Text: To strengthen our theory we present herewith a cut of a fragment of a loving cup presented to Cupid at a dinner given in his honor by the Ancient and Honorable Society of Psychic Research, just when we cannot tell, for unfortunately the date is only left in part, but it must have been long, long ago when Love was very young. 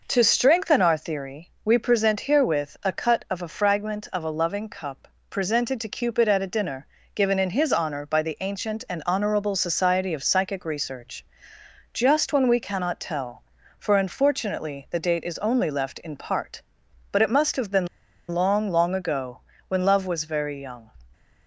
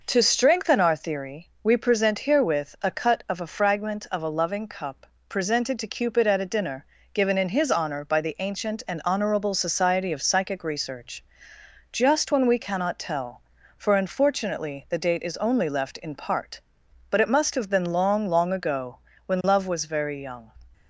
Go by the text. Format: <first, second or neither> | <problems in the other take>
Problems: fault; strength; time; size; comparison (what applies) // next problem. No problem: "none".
second | pauses between "cup" and "presented"; slight; at 5.0 s; 0.22 s long; slight in the second // pauses between "dinner" and "given"; slight; at 6.8 s; 0.30 s long; slight in the second // pauses between "been" and "long"; at 17.8 s; 0.43 s long // pauses between "ago" and "when"; slight; at 19.4 s; 0.28 s long; slight in the second